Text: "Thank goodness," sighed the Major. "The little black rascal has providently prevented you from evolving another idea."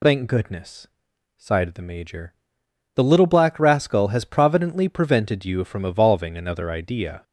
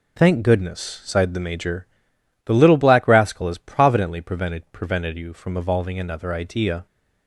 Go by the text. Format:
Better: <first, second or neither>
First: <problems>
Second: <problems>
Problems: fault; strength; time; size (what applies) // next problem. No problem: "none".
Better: first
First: none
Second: says "prevented" twice; at 4.7 s